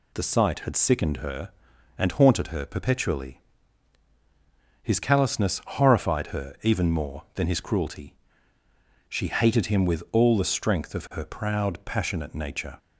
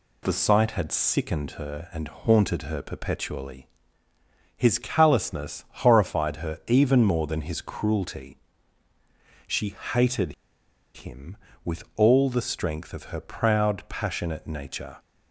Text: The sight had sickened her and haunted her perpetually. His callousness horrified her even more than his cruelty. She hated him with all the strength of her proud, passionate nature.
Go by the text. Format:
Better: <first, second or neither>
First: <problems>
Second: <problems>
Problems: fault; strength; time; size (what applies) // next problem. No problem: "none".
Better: first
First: none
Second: pauses between "She" and "hated"; slight; at 9.7 s; 0.18 s long // pauses between "hated" and "him"; noticeable; at 10.3 s; 0.62 s long